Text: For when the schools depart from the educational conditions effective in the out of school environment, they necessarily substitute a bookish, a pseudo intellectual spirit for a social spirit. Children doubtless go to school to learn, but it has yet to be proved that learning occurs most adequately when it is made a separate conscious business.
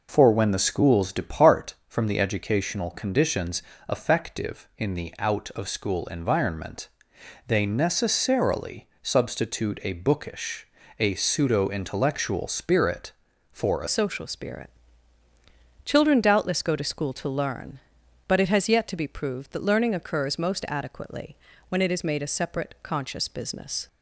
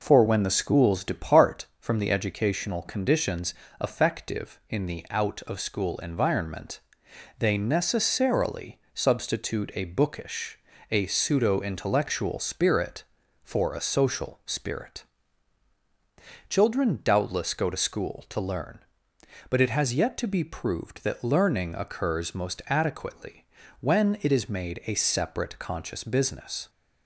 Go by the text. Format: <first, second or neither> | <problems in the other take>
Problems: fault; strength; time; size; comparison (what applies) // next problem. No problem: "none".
second | pauses between "conditions" and "effective"; slight; at 3.6 s; 0.26 s long; slight in the second // pauses between "necessarily" and "substitute"; slight; at 8.8 s; 0.16 s long; slight in the second // changes voice at "social"; from 13.8 s on; 10.0 s long // pauses between "adequately" and "when"; slight; at 21.3 s; 0.34 s long; slight in the second